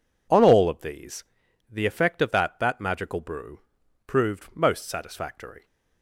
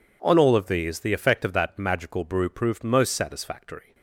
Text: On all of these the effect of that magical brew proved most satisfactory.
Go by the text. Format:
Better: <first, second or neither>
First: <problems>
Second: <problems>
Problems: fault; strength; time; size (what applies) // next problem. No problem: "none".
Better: second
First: pauses between "these" and "the"; noticeable; at 1.2 s; 0.48 s long // says "that" twice; at 2.5 s // pauses between "brew" and "proved"; noticeable; at 3.5 s; 0.48 s long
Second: none